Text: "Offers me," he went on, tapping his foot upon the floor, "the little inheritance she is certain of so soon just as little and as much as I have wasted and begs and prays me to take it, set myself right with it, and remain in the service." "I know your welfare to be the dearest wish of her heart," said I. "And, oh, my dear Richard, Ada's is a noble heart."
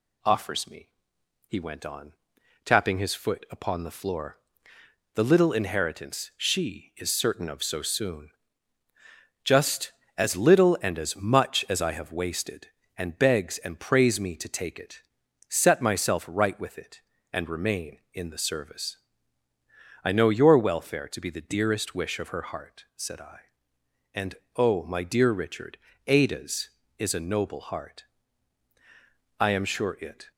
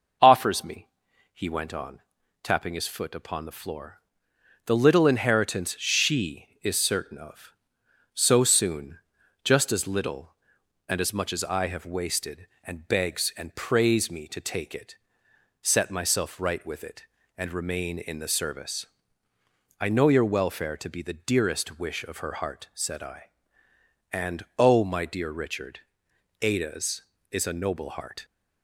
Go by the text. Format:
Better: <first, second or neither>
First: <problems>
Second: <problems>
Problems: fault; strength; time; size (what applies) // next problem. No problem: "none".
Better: second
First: pauses between "soon" and "just"; at 8.3 s; 1.1 s long // goes on to say "I am sure it"; noticeable; from 29.3 s on; 0.92 s long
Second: pauses between "soon" and "just"; noticeable; at 8.9 s; 0.46 s long